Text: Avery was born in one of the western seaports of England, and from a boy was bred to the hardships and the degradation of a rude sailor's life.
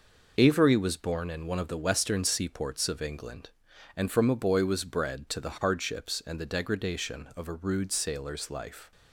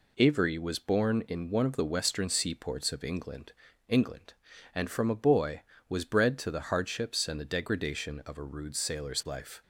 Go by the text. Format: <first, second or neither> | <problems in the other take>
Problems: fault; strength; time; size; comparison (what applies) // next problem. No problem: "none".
first | says "England" twice; at 3.8 s